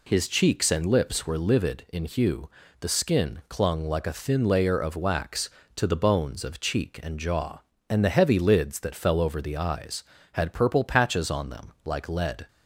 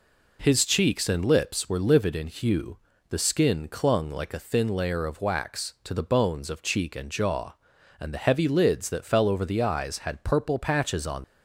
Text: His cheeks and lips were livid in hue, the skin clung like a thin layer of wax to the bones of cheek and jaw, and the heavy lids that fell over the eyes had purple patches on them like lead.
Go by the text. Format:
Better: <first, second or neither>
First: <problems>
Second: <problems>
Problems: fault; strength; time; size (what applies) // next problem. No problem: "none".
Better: first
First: none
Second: stops before "them like lead"; at 11.2 s